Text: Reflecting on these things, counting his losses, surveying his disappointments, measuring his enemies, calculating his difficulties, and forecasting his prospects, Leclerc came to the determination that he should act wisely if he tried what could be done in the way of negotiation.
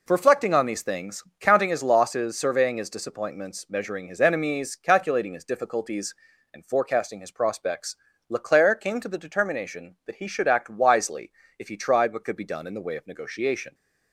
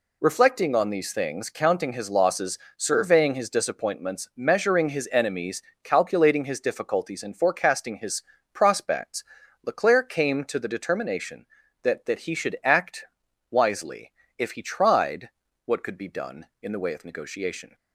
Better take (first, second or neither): first